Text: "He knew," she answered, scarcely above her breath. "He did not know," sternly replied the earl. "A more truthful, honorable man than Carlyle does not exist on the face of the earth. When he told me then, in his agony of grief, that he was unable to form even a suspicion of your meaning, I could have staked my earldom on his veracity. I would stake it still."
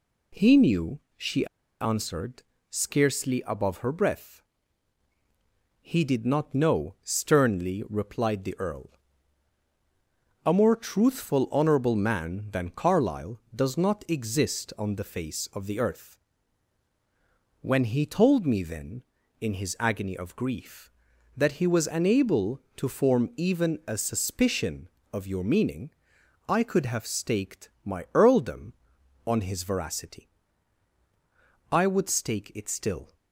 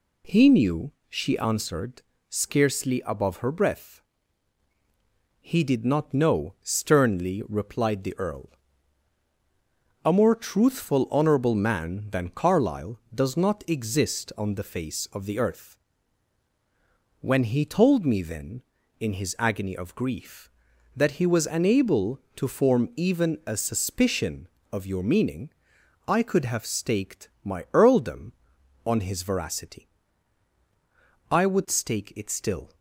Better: second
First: pauses between "she" and "answered"; slight; at 1.4 s; 0.35 s long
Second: none

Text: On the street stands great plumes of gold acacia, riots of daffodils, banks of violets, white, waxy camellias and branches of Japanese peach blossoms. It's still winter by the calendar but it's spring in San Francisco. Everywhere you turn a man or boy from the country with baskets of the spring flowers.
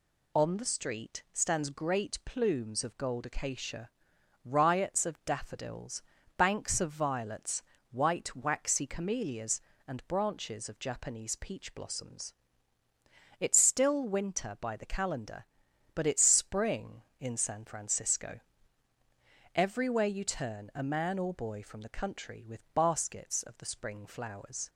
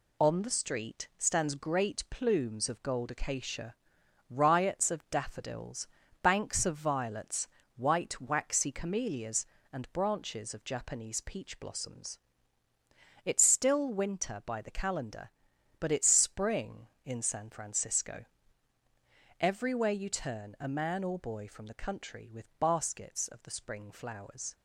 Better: first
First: none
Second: gets quieter; noticeable; throughout; 5 dB

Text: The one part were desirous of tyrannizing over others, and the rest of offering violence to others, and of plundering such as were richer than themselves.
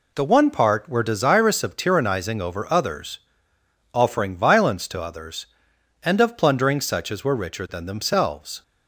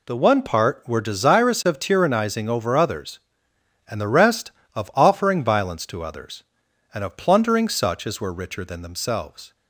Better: second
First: skips "and the rest of"; at 3.5 s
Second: none

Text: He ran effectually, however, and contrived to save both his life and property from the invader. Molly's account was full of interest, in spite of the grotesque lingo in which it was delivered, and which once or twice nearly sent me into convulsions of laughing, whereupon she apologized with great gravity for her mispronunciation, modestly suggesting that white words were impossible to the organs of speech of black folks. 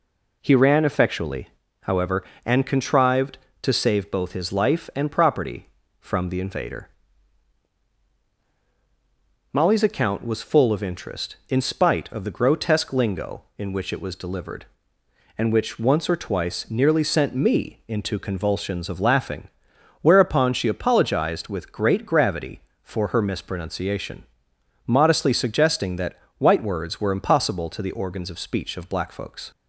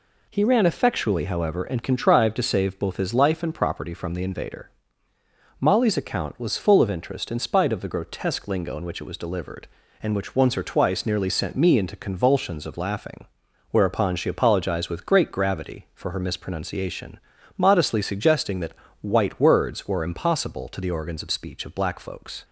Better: neither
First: pauses between "that" and "white"; slight; at 26.1 s; 0.22 s long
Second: pauses between "that" and "white"; slight; at 18.7 s; 0.28 s long

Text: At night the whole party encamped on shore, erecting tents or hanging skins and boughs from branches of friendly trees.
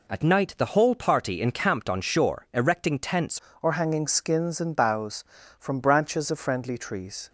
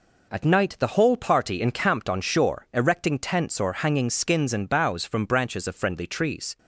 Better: second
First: changes voice at "or"; from 3.6 s on; 3.6 s long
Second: none

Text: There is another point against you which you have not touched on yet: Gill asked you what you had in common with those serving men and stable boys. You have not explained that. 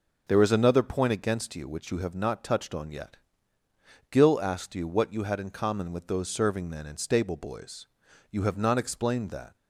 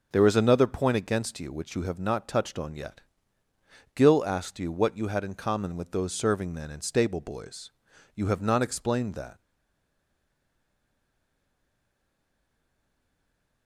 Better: first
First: none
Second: stays silent after the last word; strong; from 9.3 s on; 4.3 s long

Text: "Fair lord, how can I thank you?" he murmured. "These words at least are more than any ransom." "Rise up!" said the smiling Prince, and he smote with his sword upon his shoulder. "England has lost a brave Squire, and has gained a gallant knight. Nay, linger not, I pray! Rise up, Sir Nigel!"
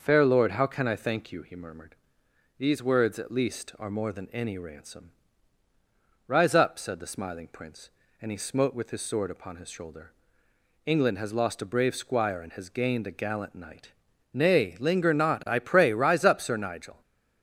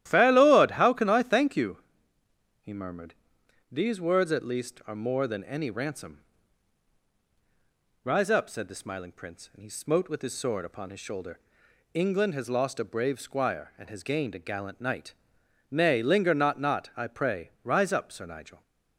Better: first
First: starts louder than the rest; noticeable; until 1.0 s; 6 dB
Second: starts louder than the rest; strong; until 1.1 s; 13 dB // says "not" twice; at 16.5 s

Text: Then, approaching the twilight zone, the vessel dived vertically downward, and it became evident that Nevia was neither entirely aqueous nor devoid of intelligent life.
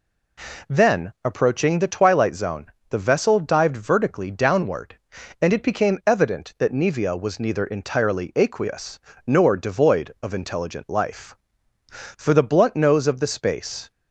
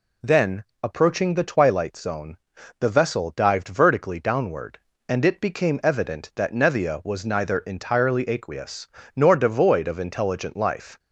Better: second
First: pauses between "aqueous" and "nor"; slight; at 9.0 s; 0.26 s long // goes on to say "For the blunt nose of the space"; strong; from 11.9 s on; 2.0 s long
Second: pauses between "aqueous" and "nor"; slight; at 8.8 s; 0.28 s long

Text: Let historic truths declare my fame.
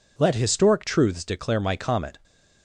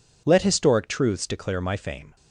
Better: second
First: says "comet" for "fame"; at 1.7 s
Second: none

